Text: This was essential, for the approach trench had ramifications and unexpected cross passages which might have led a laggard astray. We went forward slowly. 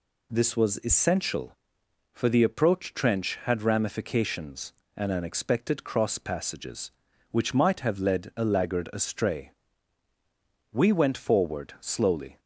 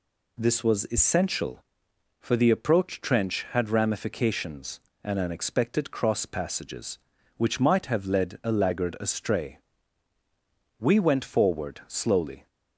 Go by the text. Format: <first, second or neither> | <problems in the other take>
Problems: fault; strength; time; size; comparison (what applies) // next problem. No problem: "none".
neither | none